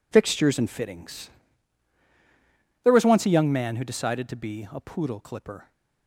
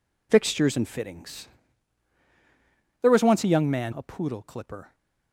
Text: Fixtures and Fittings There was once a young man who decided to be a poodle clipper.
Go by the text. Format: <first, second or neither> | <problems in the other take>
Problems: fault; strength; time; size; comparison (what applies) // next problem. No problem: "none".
first | pauses between "Fittings" and "There"; strong; at 1.4 s; 1.5 s long; strong in the first // skips "who decided to be"; at 3.9 s